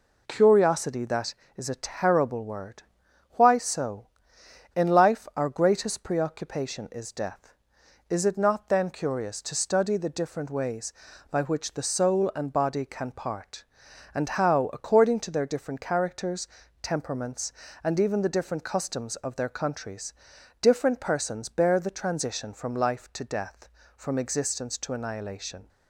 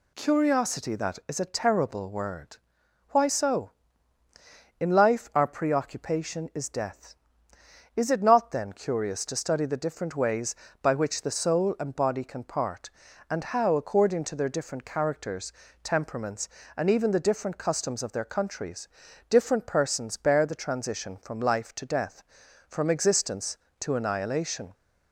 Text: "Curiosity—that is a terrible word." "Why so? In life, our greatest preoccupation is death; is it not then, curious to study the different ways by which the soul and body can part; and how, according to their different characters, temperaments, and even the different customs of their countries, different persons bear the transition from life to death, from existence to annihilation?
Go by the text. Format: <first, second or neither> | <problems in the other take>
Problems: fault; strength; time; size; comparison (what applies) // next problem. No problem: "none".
first | skips "greatest"; at 5.4 s